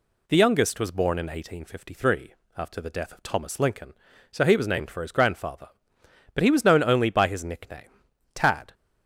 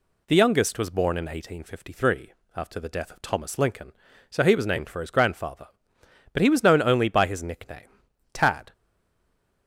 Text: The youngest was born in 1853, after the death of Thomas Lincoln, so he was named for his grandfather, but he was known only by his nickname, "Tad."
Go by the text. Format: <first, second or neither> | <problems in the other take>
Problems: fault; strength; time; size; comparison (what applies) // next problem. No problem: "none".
first | stays silent after the last word; slight; from 8.7 s on; 0.9 s long